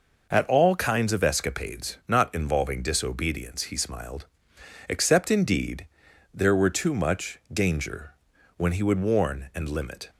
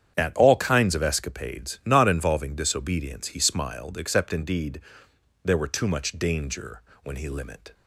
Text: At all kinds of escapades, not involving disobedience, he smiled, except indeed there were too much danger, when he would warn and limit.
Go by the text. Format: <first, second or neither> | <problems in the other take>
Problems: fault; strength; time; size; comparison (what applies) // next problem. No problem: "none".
first | starts louder than the rest; strong; until 1.1 s; 9 dB // pauses between "indeed" and "there"; noticeable; at 4.7 s; 0.64 s long; noticeable in the first // skips "would warn and"; at 7.2 s